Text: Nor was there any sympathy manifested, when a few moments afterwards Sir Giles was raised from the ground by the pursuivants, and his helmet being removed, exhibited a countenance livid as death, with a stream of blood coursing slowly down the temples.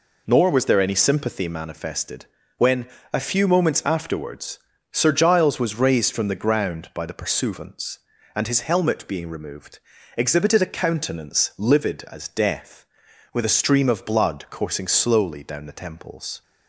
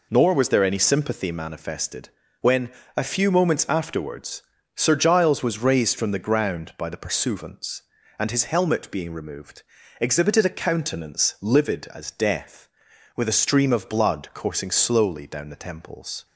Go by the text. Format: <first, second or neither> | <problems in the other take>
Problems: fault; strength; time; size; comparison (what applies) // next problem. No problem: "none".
neither | pauses between "when" and "a"; slight; the same in both // pauses between "afterwards" and "Sir"; slight; the same in both